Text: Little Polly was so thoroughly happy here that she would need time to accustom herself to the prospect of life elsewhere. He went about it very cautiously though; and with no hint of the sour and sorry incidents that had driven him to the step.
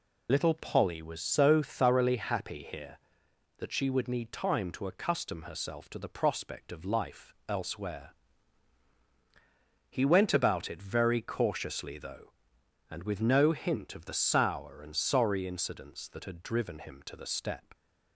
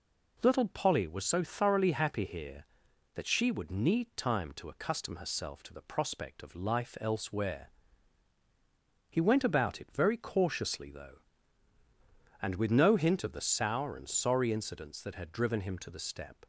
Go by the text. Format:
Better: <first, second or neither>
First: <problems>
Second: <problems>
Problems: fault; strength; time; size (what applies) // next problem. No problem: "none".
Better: second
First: loses the start of "Little"; at 0.2 s; 35 ms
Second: none